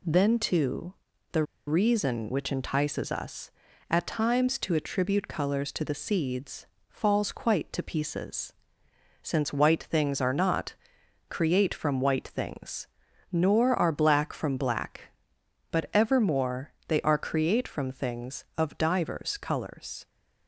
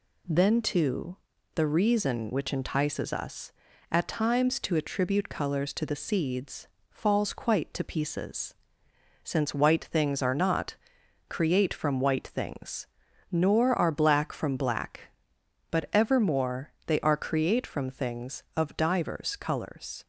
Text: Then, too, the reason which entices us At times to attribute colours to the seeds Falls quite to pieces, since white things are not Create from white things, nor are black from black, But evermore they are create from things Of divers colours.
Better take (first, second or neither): second